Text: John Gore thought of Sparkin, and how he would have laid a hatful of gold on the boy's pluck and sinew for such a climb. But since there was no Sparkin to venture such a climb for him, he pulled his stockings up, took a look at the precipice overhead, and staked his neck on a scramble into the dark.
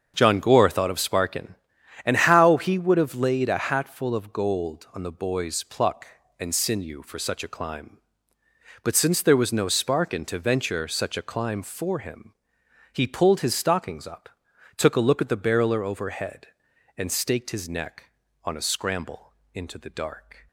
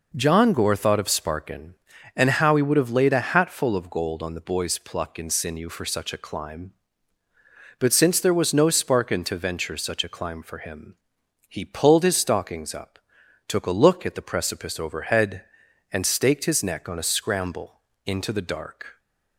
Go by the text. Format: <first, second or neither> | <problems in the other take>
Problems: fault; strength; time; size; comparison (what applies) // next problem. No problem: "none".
second | starts louder than the rest; until 1.1 s; 7 dB // says "barreler" for "precipice"; at 15.3 s // pauses between "scramble" and "into"; slight; at 19.3 s; 0.20 s long; slight in the second